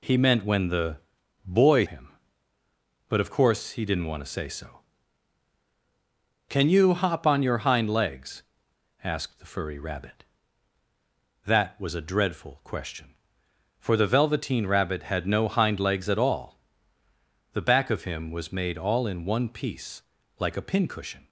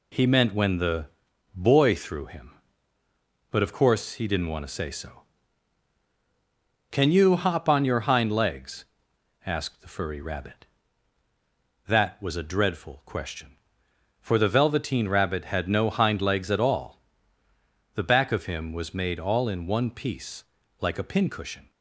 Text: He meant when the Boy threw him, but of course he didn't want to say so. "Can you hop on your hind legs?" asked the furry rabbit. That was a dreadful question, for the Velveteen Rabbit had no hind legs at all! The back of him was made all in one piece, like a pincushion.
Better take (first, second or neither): second